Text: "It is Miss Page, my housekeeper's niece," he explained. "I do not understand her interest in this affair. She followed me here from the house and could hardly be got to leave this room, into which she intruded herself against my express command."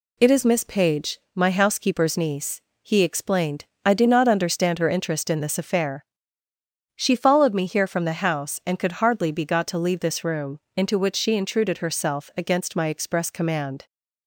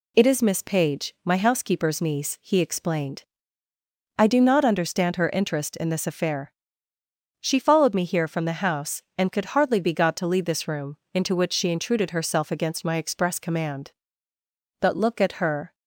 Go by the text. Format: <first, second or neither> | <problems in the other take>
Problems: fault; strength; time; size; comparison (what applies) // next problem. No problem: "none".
first | goes on to say "But look at her"; noticeable; from 14.7 s on; 0.96 s long